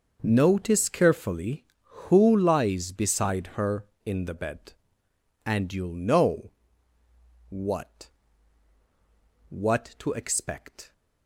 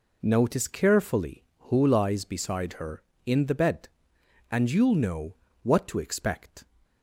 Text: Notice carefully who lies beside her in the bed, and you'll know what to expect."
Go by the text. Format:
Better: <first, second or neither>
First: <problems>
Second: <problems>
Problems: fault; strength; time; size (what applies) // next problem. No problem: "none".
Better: second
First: starts louder than the rest; noticeable; until 1.2 s; 6 dB // pauses between "know" and "what"; noticeable; at 6.5 s; 0.98 s long // says "what" twice; at 9.4 s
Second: pauses between "know" and "what"; slight; at 5.3 s; 0.28 s long